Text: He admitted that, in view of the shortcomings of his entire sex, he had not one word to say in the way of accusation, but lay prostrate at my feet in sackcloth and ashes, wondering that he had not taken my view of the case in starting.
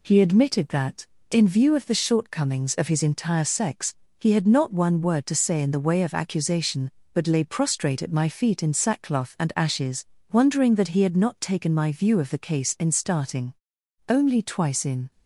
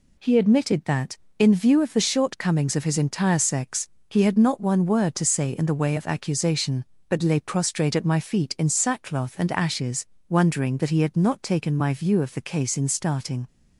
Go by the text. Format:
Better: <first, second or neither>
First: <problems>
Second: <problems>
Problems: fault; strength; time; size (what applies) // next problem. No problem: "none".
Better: second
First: goes on to say "Only twice in"; noticeable; from 14.0 s on; 1.0 s long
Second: none